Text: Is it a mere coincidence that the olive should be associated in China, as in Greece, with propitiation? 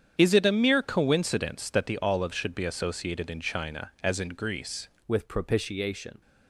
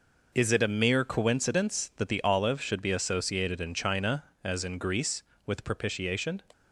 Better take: second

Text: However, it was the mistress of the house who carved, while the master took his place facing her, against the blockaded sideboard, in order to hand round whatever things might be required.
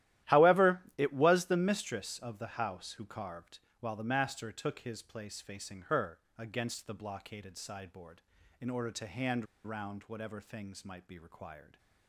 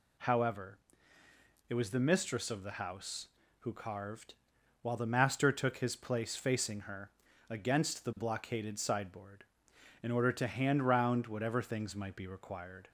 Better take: second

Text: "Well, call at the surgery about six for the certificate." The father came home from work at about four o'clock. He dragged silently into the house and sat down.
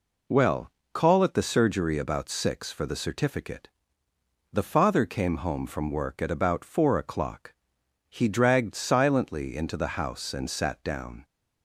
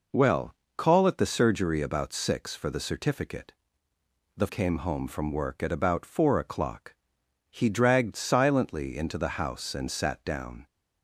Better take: first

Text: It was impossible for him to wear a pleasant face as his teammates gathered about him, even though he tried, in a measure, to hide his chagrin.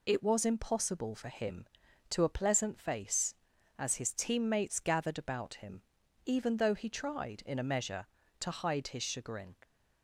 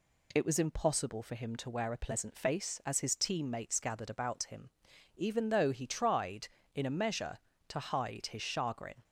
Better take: second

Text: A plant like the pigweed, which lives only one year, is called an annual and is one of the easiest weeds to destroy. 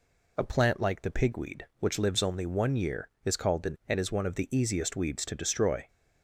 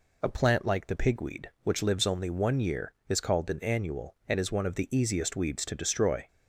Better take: second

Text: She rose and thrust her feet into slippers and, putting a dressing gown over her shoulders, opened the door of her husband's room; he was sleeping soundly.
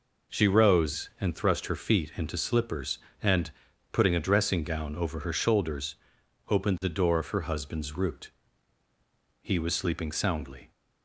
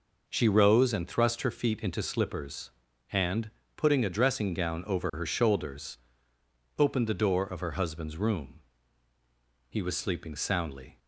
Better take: second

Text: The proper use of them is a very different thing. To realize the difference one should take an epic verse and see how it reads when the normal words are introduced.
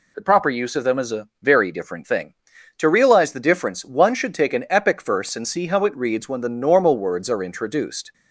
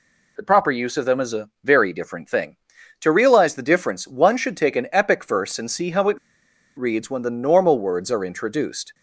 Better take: first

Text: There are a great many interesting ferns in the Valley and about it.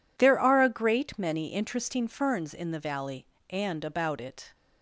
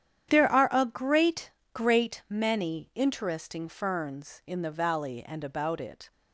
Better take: first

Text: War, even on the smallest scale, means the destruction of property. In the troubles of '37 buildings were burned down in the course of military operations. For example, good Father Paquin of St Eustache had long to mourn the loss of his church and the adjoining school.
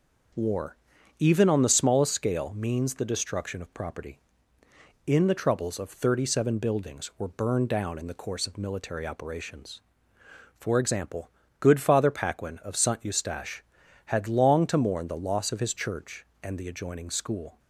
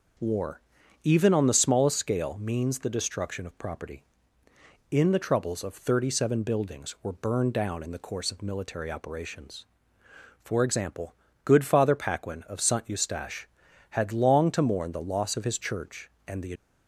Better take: first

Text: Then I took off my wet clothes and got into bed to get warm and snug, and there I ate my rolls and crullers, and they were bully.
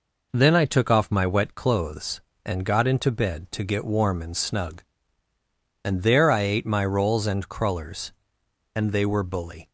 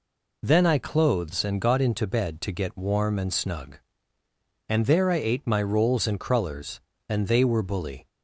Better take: first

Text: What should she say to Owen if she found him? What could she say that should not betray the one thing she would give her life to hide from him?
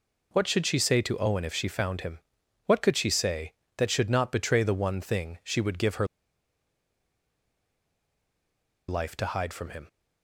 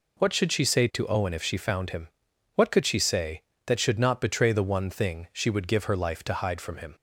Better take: second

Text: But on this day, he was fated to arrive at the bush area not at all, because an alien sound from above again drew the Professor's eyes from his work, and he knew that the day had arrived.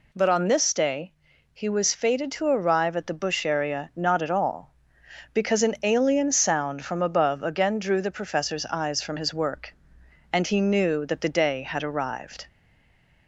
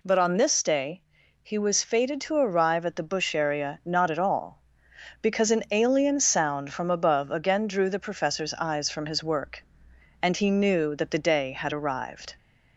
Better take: second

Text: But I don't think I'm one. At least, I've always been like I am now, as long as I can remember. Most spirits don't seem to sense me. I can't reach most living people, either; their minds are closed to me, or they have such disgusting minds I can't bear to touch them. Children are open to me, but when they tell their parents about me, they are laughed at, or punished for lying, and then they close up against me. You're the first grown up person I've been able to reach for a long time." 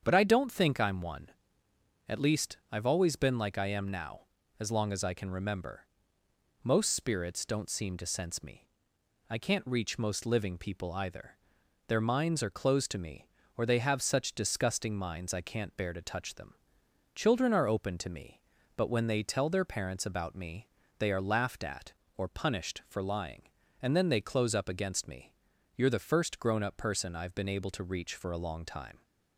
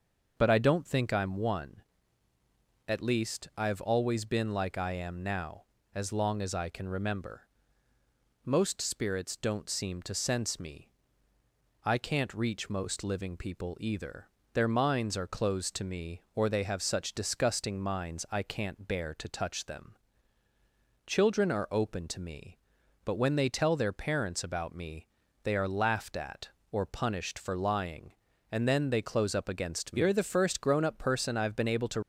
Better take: first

